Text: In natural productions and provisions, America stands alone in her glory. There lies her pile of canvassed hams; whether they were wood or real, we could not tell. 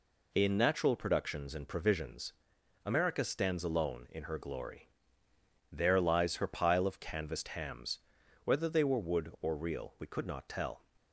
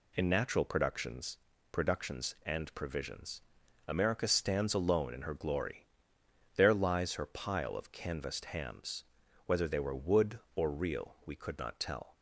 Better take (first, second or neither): first